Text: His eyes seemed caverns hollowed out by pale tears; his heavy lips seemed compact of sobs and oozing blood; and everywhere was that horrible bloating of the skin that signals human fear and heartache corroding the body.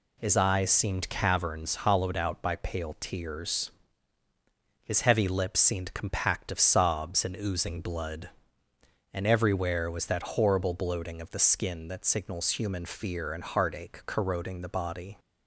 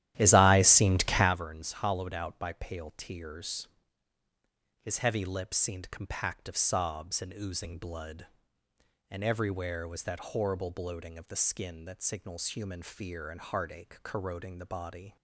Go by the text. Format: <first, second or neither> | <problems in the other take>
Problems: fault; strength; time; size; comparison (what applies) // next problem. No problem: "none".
first | starts louder than the rest; strong; until 1.4 s; 12.5 dB